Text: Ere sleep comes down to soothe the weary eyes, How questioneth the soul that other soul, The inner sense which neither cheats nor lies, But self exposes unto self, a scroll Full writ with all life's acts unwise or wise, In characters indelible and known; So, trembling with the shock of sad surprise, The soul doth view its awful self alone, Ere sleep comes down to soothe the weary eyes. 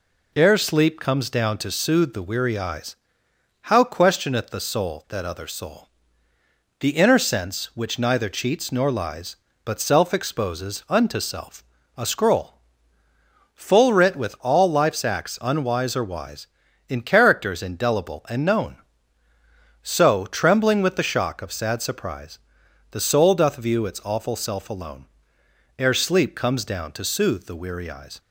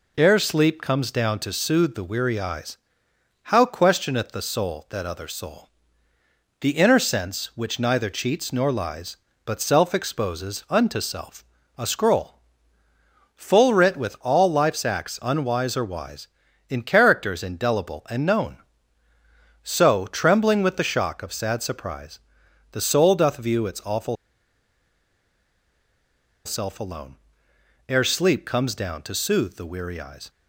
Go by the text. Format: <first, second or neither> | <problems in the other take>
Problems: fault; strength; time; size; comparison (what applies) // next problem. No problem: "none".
first | pauses between "scroll" and "Full"; noticeable; at 12.3 s; 0.96 s long; noticeable in the first // pauses between "awful" and "self"; strong; at 24.1 s; 2.3 s long